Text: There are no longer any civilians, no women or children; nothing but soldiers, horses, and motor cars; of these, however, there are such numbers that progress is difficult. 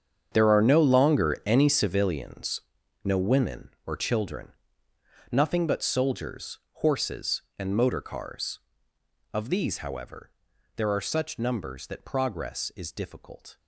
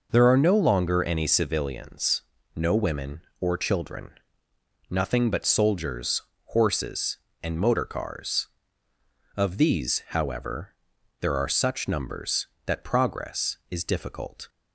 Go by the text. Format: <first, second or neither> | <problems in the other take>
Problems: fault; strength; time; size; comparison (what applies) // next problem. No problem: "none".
second | gets quieter; strong; throughout; 15.5 dB